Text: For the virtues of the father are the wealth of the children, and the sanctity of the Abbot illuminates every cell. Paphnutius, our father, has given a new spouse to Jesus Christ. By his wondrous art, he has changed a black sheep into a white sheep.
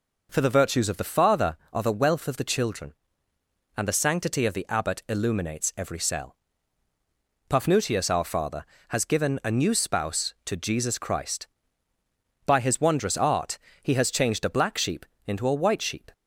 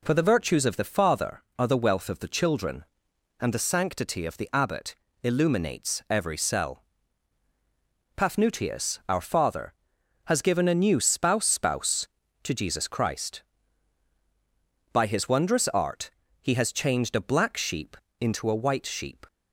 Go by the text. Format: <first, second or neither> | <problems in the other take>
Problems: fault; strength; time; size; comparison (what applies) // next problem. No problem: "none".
first | pauses between "Abbot" and "illuminates"; slight; at 4.9 s; 0.26 s long // says "spouse" twice; at 11.4 s // pauses between "sheep" and "into"; slight; at 17.9 s; 0.24 s long; slight in the first